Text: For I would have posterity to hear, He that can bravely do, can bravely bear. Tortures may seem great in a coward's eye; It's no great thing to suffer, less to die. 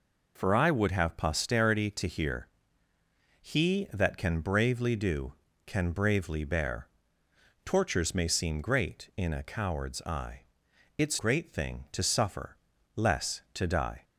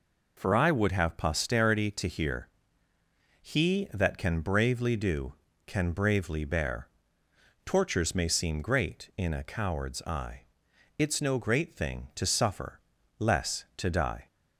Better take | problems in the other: second | skips "no"; at 11.1 s

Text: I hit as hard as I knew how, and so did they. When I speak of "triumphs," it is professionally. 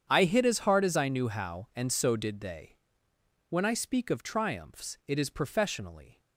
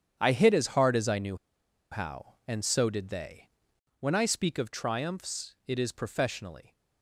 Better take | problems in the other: first | starts louder than the rest; strong; until 1.2 s; 9 dB; strong in the first // pauses between "knew" and "how"; noticeable; at 1.3 s; 0.56 s long

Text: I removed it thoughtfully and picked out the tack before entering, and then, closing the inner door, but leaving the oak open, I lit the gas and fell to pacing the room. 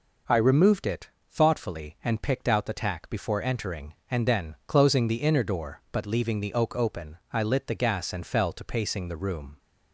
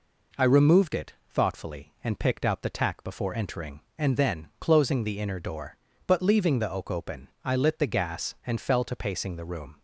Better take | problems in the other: neither | pauses between "it" and "thoughtfully"; slight; the same in both

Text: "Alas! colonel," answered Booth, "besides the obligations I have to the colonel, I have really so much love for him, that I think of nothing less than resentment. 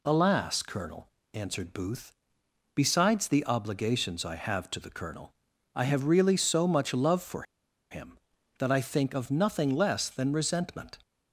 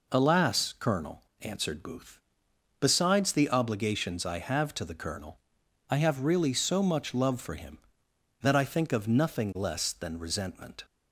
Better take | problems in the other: second | pauses between "for" and "him"; noticeable; at 7.4 s; 0.48 s long

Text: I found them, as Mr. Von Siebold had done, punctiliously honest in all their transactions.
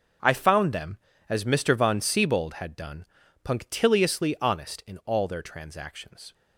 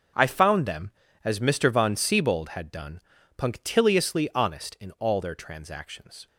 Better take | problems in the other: neither | none

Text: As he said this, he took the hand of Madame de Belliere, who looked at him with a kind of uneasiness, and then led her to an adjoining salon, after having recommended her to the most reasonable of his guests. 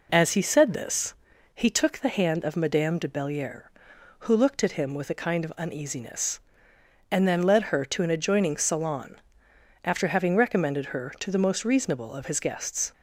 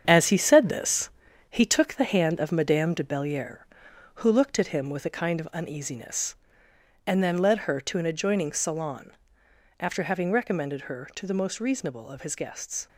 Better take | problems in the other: first | gets quieter; throughout; 7 dB

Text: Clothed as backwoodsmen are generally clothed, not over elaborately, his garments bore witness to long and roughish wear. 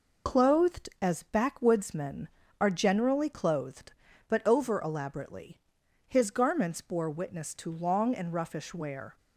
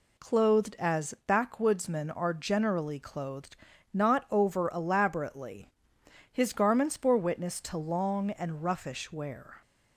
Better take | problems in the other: second | says "but" for "not"; at 4.2 s

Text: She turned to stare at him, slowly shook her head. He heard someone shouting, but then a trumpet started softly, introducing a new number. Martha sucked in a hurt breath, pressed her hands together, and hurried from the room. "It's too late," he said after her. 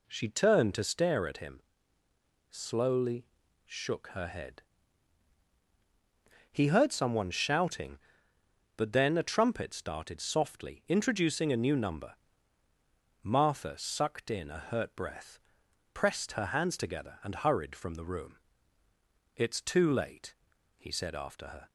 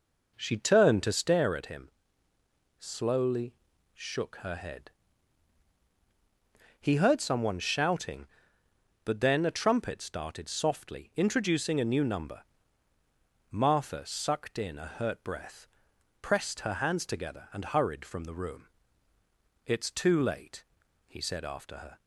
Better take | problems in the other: first | starts louder than the rest; noticeable; until 1.6 s; 5 dB // pauses between "slowly" and "shook"; at 3.5 s; 0.40 s long; also in the first

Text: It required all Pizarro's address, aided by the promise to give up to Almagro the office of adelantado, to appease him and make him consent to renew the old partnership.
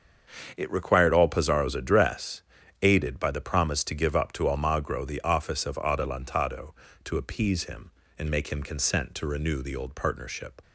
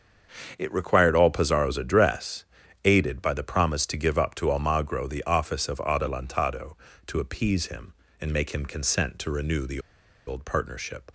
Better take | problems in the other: first | starts louder than the rest; until 1.5 s; 7 dB; also in the first // pauses between "the" and "old"; noticeable; at 9.7 s; 0.47 s long

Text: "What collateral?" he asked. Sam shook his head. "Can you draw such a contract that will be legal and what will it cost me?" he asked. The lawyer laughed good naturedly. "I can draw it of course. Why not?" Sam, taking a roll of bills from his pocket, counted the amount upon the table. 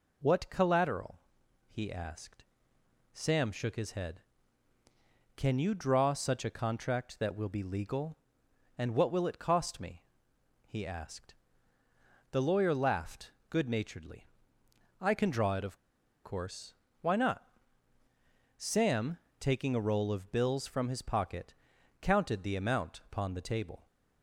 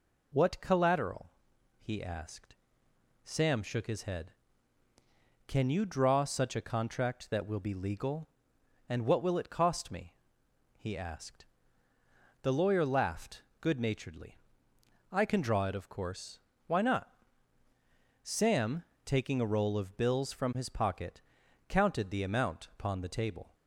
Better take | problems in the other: second | pauses between "laughed" and "good"; slight; at 13.3 s; 0.18 s long; slight in the second // pauses between "of" and "course"; at 15.7 s; 0.45 s long

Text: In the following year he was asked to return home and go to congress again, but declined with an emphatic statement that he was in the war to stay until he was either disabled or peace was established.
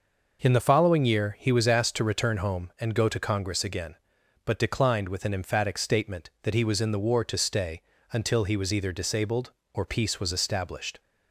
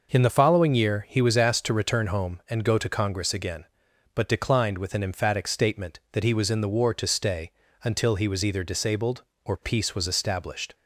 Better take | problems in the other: neither | pauses between "stay" and "until"; slight; the same in both

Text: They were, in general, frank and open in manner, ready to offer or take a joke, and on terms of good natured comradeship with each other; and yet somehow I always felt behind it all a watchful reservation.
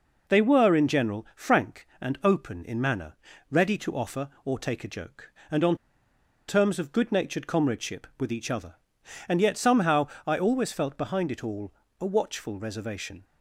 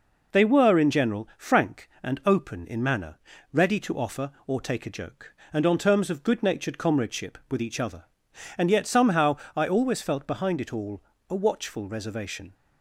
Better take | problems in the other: second | pauses between "on" and "terms"; noticeable; at 5.7 s; 0.73 s long // pauses between "somehow" and "I"; slight; at 10.0 s; 0.20 s long; slight in the second // pauses between "all" and "a"; slight; at 11.7 s; 0.28 s long; slight in the second

